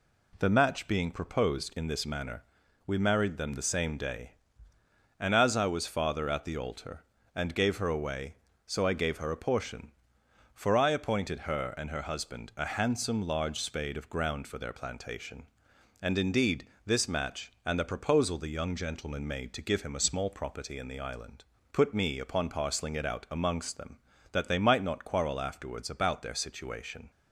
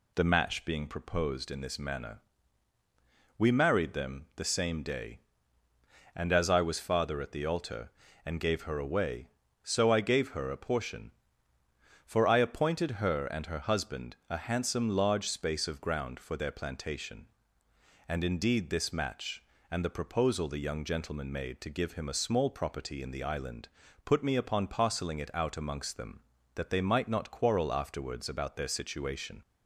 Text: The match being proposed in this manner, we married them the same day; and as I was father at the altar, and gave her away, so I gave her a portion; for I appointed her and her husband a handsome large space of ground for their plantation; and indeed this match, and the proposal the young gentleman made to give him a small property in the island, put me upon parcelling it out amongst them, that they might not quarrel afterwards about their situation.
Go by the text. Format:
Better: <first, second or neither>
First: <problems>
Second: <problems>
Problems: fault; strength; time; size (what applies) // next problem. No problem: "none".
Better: second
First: says "spade" for "space"; at 13.5 s // pauses between "indeed" and "this"; slight; at 16.6 s; 0.18 s long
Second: none